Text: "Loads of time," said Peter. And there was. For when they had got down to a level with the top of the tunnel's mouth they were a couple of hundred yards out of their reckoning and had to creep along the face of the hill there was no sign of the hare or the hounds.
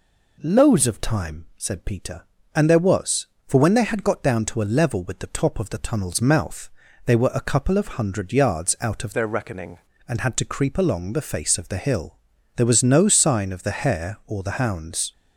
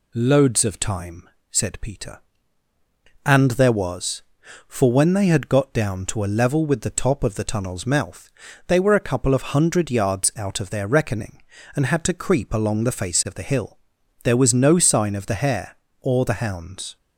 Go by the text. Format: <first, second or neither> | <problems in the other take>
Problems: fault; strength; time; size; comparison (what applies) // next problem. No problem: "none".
second | pauses between "mouth" and "they"; at 6.6 s; 0.38 s long; also in the second // changes voice from "their" to "reckoning"; from 9.1 to 9.7 s; 0.6 s long // pauses between "hill" and "there"; at 12.1 s; 0.40 s long; noticeable in the second